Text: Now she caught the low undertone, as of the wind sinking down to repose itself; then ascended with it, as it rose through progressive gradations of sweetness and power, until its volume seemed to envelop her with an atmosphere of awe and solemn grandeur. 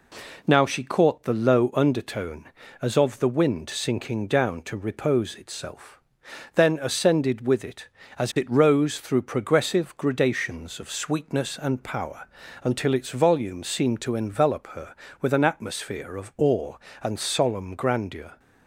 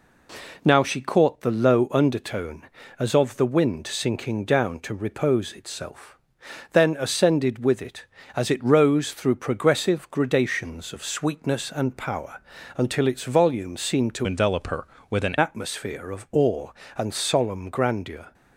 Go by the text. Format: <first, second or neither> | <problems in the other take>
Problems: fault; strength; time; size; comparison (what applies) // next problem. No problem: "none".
first | changes voice from "envelop" to "an"; from 14.2 to 15.3 s; 1.1 s long